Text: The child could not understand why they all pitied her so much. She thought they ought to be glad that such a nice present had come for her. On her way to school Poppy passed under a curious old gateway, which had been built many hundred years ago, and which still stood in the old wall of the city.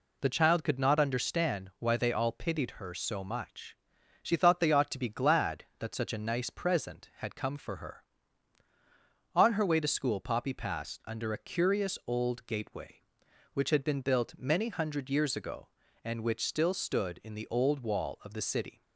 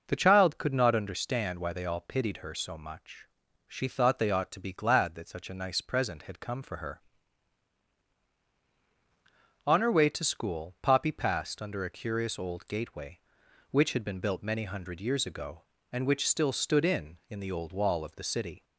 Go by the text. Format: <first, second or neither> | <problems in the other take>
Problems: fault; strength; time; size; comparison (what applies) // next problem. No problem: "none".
first | says "in" twice; at 17.2 s